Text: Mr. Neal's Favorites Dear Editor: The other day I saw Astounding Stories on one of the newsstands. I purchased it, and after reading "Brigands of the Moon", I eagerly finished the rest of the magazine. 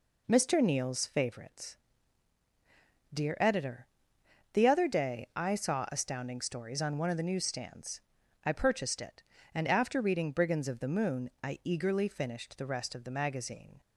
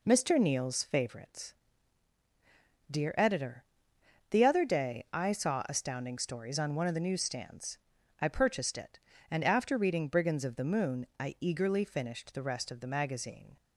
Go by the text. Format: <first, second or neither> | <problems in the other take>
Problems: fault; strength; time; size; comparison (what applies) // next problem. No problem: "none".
neither | pauses between "Favorites" and "Dear"; strong; the same in both